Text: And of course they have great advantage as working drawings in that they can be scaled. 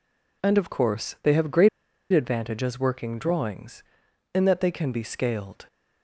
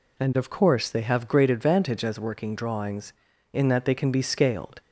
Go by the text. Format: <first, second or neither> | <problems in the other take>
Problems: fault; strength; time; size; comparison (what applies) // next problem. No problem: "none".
second | pauses between "great" and "advantage"; at 1.6 s; 0.44 s long